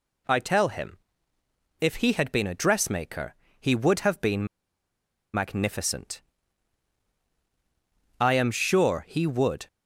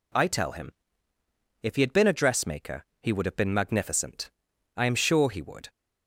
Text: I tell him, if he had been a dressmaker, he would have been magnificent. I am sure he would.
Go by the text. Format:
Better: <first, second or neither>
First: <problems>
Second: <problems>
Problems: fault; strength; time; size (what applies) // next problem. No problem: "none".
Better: second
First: pauses between "been" and "magnificent"; noticeable; at 4.4 s; 0.87 s long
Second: none